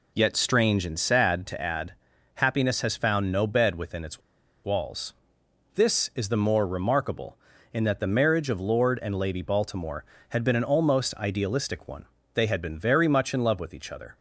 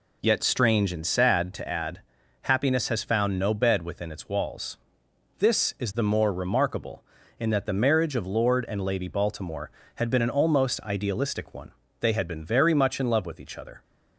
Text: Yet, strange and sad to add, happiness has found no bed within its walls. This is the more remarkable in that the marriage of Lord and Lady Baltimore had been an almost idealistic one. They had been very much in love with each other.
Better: second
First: pauses between "its" and "walls"; at 4.2 s; 0.43 s long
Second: none

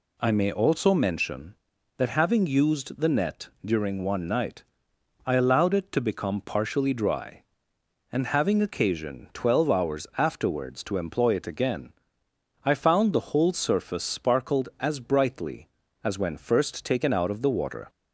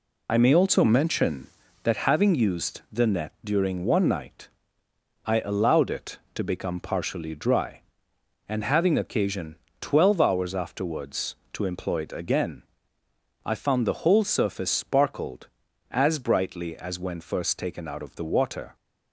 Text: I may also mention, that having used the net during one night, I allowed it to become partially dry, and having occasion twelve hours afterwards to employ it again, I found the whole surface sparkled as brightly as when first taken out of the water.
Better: first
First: none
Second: loses the start of "I"; at 0.2 s; 55 ms // pauses between "occasion" and "twelve"; slight; at 9.5 s; 0.24 s long

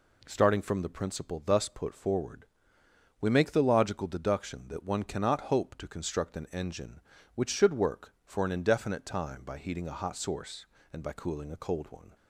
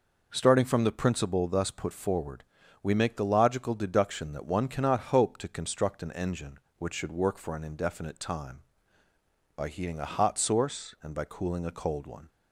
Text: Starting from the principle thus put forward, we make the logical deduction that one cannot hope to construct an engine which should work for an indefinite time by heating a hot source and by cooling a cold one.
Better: neither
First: none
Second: none

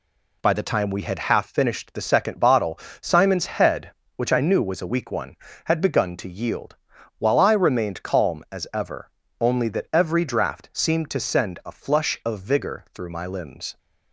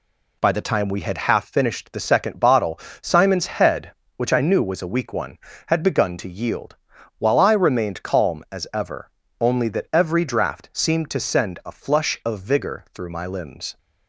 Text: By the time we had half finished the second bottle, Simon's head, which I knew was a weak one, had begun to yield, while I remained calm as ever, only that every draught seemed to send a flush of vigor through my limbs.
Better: neither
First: none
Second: none

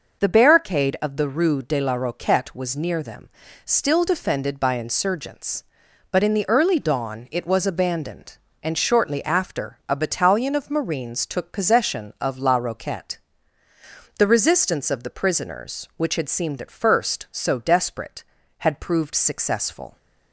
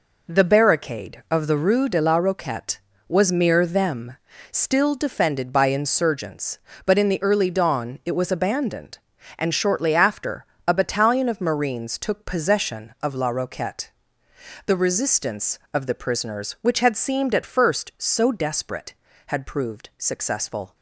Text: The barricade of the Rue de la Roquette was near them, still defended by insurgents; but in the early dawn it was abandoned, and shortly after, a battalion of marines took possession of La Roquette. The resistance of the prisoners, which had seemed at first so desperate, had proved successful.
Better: first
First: none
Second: says "mere" for "near"; at 3.3 s

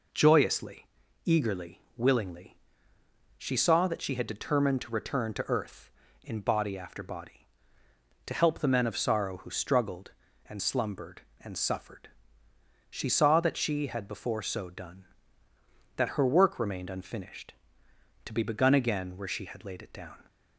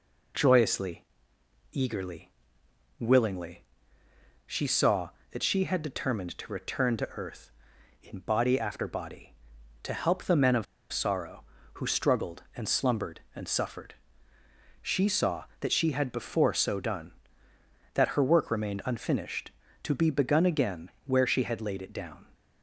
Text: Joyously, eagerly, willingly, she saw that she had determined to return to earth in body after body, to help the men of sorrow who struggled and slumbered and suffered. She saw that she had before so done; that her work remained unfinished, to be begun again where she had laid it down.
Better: first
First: none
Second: pauses between "of" and "sorrow"; slight; at 10.6 s; 0.27 s long // pauses between "again" and "where"; slight; at 20.9 s; 0.16 s long

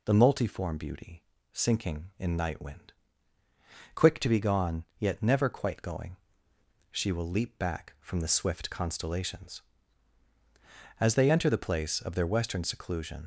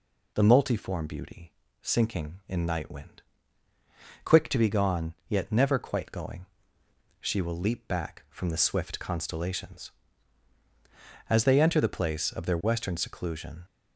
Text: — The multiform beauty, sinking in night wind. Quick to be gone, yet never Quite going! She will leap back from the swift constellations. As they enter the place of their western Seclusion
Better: second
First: leaves "Seclusion" unfinished; at 13.2 s; 50 ms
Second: none

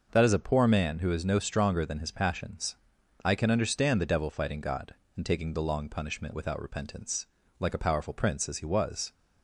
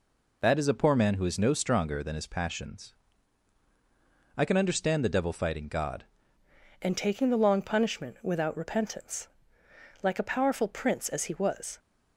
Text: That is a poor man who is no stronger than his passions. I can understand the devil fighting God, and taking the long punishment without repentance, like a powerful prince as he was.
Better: first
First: none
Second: changes voice at "and"; from 6.8 s on; 4.9 s long

